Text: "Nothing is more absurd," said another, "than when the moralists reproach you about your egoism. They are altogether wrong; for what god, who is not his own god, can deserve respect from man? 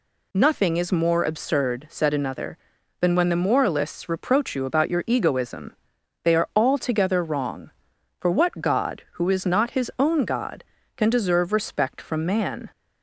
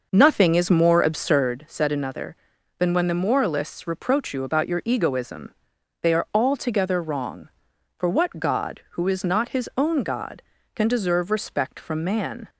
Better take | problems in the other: first | starts louder than the rest; noticeable; until 1.6 s; 6 dB

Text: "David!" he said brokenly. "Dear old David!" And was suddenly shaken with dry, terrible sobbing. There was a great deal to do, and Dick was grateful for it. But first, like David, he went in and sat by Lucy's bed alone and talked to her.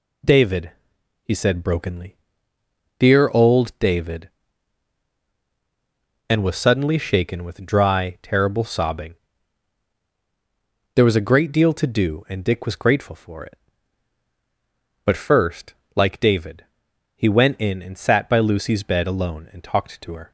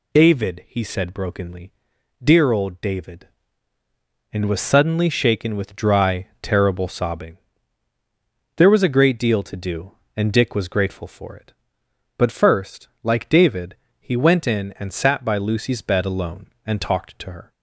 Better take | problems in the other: neither | none

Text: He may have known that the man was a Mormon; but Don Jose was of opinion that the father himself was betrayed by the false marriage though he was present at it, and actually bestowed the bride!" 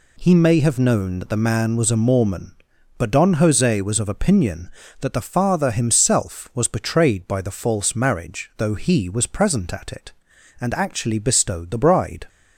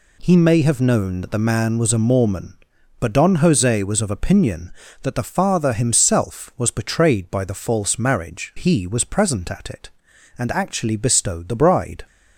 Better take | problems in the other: first | skips "though"; at 8.5 s

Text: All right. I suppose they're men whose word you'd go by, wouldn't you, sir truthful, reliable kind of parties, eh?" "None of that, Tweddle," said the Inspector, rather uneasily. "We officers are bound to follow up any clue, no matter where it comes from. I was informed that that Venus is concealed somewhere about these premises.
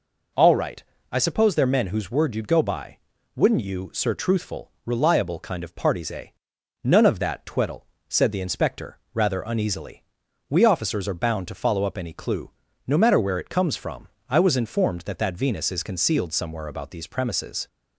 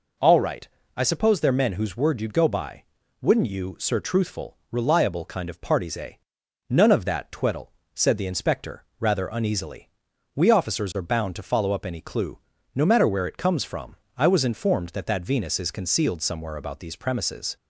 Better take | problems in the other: neither | none

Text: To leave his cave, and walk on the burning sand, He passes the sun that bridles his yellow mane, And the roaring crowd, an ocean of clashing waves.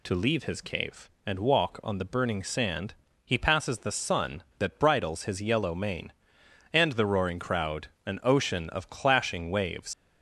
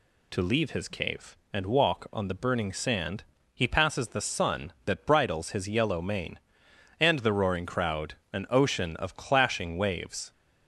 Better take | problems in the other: second | leaves "waves" unfinished; at 9.9 s; 120 ms

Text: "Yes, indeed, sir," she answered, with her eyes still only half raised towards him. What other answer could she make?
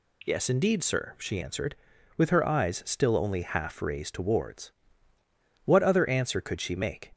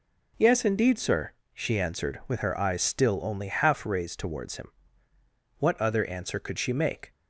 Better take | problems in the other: second | skips "him"; at 5.1 s

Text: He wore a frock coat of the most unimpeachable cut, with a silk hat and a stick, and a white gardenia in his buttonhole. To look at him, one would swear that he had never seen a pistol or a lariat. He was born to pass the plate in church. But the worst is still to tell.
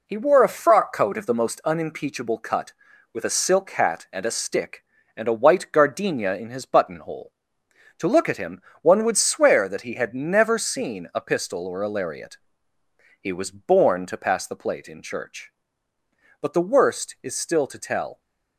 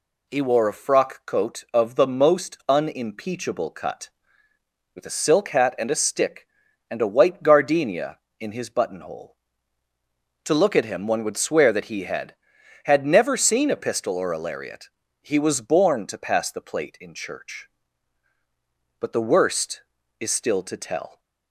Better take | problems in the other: first | says "had" twice; at 12.8 s

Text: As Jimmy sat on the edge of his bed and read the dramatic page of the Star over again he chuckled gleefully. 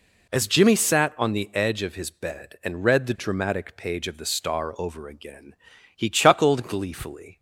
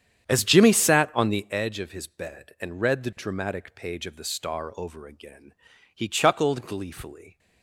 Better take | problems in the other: first | starts louder than the rest; strong; until 1.5 s; 9 dB // pauses between "again" and "he"; at 5.5 s; 0.40 s long; also in the first

